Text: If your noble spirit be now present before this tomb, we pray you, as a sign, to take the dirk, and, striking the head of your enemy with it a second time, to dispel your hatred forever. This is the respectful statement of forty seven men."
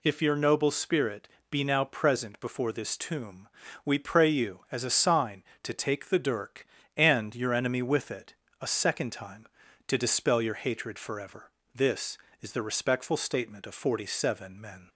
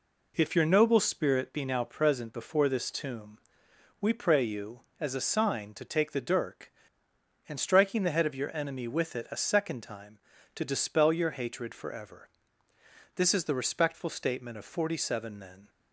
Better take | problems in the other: second | pauses between "spirit" and "be"; slight; at 1.2 s; 0.24 s long // skips "striking the head of"; at 7.3 s // pauses between "it" and "a"; slight; at 8.3 s; 0.26 s long

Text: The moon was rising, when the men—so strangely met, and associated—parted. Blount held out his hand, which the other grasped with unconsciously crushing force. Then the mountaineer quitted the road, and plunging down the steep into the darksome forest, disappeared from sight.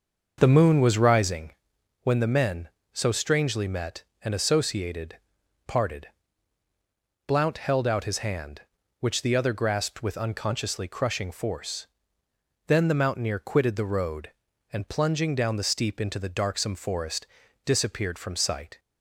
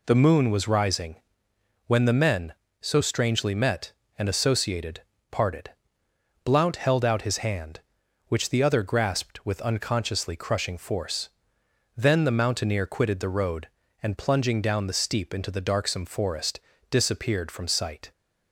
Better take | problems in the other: second | starts louder than the rest; until 1.6 s; 6 dB

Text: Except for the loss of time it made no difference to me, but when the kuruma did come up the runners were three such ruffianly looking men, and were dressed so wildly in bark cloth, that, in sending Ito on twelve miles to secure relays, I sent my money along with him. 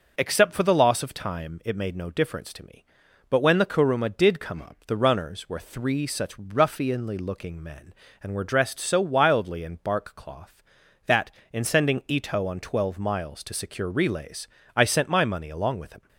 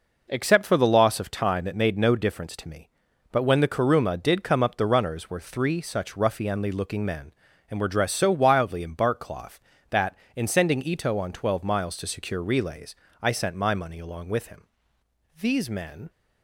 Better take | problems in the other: first | goes on to say "These men"; noticeable; from 15.3 s on; 0.72 s long

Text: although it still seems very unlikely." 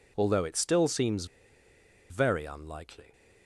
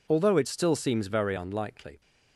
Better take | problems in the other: second | pauses between "seems" and "very"; noticeable; at 1.2 s; 0.84 s long

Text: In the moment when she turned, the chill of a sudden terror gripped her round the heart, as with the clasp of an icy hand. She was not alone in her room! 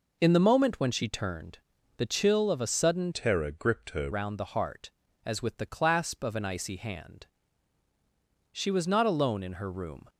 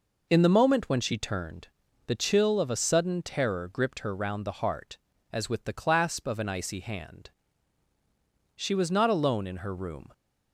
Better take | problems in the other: second | changes voice from "terror" to "her"; from 3.1 to 4.1 s; 1.0 s long

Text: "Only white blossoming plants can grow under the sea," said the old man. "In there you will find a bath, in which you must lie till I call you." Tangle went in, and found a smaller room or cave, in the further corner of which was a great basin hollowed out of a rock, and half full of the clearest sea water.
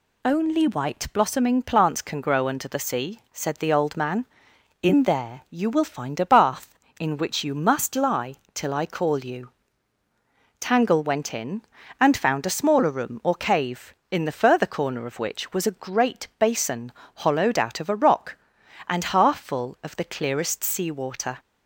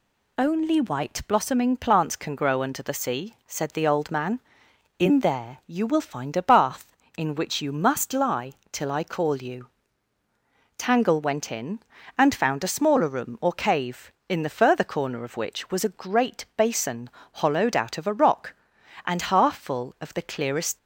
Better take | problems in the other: first | pauses between "lie" and "till"; slight; at 8.5 s; 0.18 s long; slight in the first // pauses between "basin" and "hollowed"; slight; at 17.0 s; 0.32 s long; slight in the first // stops before "sea water"; at 20.7 s

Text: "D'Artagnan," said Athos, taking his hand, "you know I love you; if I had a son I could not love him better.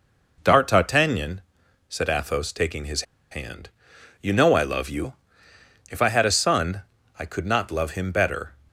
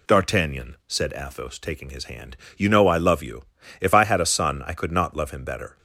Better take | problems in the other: second | pauses between "his" and "hand"; slight; at 3.0 s; 0.28 s long // pauses between "son" and "I"; at 6.8 s; 0.38 s long

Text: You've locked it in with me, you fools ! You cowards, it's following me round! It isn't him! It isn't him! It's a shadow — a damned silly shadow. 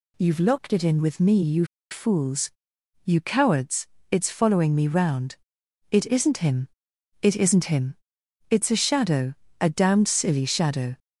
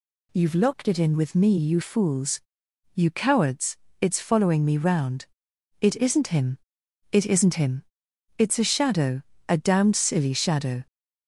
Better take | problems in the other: second | pauses between "you" and "fools"; slight; at 1.6 s; 0.26 s long

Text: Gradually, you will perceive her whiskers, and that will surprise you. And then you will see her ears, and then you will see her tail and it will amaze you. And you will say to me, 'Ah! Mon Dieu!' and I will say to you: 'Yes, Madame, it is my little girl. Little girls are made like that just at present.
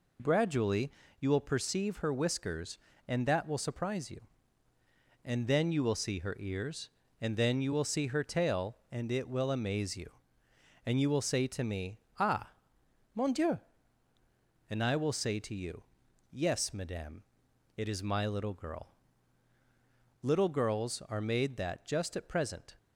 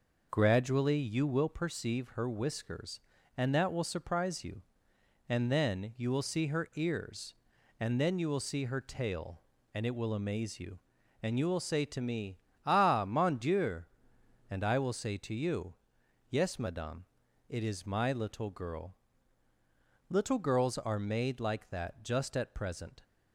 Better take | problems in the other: second | skips "like"; at 21.5 s

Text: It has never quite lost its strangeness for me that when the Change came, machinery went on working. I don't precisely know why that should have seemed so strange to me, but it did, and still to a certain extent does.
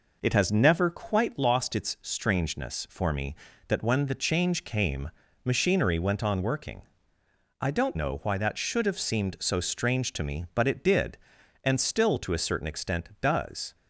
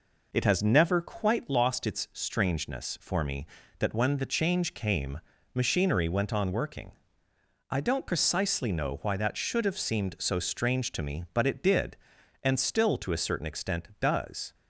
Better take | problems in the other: second | skips "precisely"; at 7.9 s

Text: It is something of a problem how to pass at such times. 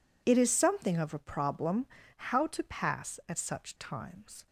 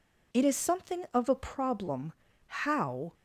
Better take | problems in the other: first | pauses between "problem" and "how"; slight; at 2.1 s; 0.32 s long; slight in the first // stops before "to pass at such times"; at 3.1 s

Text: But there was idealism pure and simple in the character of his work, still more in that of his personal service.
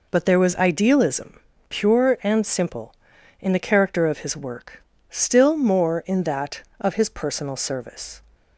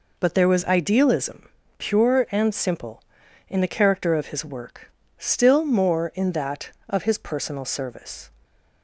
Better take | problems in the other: neither | pauses between "idealism" and "pure"; slight; the same in both

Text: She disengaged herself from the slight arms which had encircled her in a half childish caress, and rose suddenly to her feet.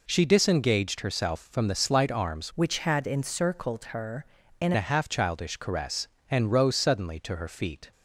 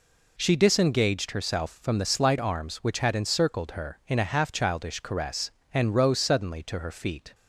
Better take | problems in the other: second | changes voice from "which" to "in"; from 2.5 to 4.7 s; 2.2 s long

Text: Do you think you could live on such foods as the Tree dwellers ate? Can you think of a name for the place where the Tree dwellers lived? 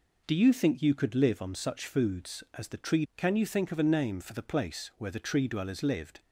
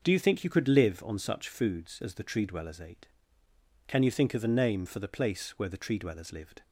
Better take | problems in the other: second | skips "dwellers ate"; at 3.0 s

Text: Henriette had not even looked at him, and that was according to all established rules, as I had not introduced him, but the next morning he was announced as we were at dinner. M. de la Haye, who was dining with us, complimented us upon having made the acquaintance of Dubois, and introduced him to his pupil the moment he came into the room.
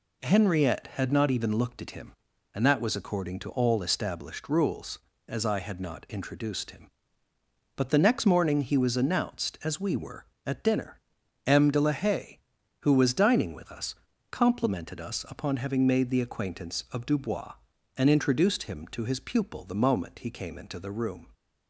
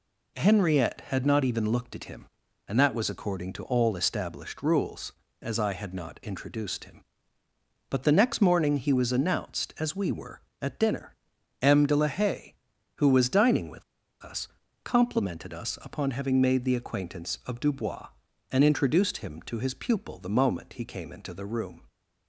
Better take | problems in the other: first | pauses between "with" and "us"; at 13.8 s; 0.40 s long

